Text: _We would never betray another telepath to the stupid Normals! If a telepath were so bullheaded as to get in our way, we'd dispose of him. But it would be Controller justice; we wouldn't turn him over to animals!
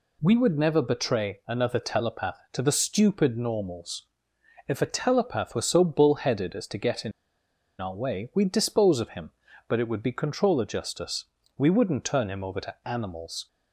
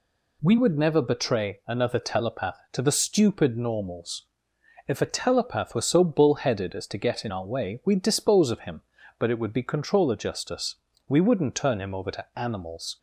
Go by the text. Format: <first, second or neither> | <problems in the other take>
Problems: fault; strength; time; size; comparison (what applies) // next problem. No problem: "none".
second | pauses between "in" and "our"; noticeable; at 7.1 s; 0.69 s long